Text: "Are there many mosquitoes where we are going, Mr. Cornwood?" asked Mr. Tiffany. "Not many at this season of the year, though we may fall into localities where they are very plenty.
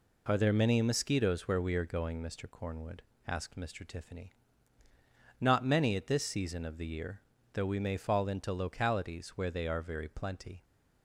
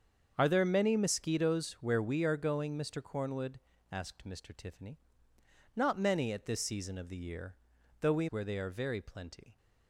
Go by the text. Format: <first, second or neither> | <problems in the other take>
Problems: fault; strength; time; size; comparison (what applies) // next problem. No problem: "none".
first | starts louder than the rest; until 1.3 s; 7 dB // skips "may fall into localities"; at 8.2 s